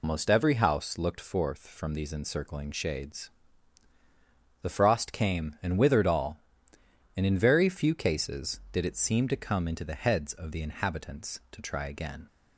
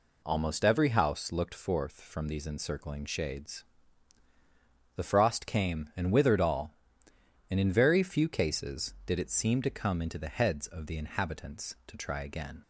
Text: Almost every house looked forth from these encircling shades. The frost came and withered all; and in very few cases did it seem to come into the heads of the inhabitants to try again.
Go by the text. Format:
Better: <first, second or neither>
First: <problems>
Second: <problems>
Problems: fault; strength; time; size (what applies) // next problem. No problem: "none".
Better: second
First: loses the start of "Almost"; at 0.0 s; 135 ms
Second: none